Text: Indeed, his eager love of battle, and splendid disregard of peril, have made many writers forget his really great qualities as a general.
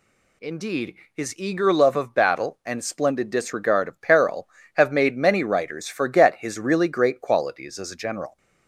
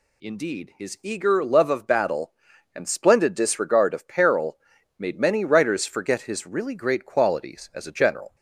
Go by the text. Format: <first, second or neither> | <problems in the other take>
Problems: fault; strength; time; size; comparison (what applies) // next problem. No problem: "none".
first | skips "have"; at 4.7 s